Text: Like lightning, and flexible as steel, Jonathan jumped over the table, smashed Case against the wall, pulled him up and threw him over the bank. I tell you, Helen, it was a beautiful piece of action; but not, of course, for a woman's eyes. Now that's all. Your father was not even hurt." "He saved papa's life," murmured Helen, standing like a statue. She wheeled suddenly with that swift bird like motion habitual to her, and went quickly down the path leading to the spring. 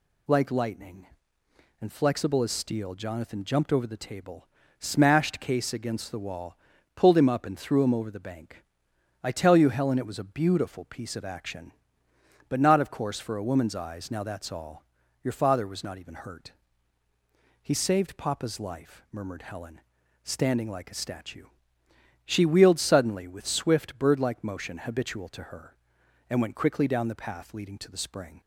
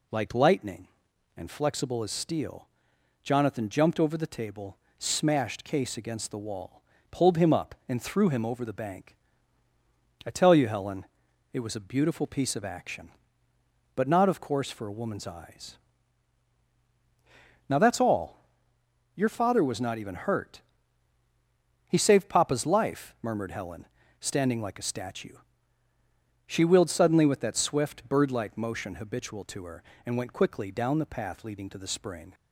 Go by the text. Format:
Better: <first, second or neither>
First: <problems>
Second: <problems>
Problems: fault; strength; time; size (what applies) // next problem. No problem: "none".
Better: second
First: skips "that"; at 23.4 s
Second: none